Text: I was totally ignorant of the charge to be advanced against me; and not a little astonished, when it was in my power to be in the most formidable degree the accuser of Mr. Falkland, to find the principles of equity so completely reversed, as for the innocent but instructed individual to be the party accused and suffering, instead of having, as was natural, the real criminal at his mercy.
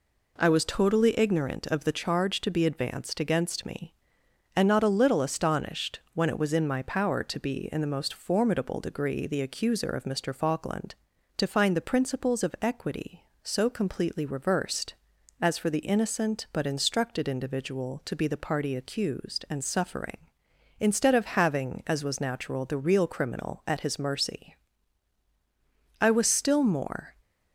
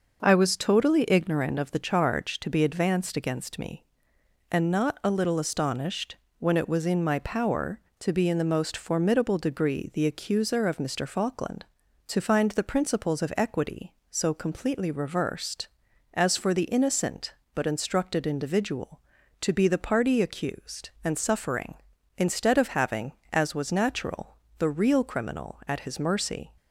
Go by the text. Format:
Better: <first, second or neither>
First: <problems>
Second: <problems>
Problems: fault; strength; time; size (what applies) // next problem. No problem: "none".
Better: second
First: goes on to say "I was still more"; noticeable; from 25.9 s on; 1.1 s long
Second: none